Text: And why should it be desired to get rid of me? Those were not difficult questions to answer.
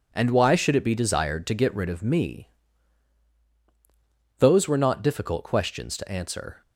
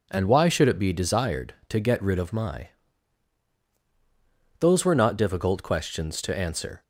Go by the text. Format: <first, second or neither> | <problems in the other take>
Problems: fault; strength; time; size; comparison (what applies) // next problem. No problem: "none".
first | says "my" for "me"; at 2.3 s